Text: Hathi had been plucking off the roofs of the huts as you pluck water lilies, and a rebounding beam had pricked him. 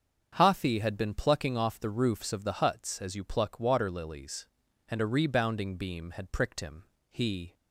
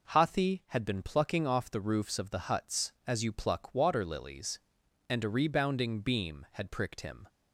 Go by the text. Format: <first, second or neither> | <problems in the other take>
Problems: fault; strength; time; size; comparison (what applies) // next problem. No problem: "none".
second | starts louder than the rest; until 1.3 s; 7 dB // goes on to say "He"; slight; from 7.1 s on; 0.42 s long